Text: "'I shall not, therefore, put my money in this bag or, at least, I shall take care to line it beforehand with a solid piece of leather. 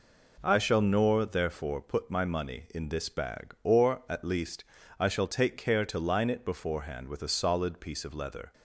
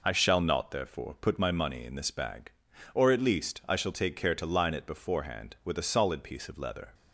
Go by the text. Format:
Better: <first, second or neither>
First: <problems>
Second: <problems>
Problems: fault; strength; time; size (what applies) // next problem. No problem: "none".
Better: second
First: says "nor" for "not"; at 0.8 s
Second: none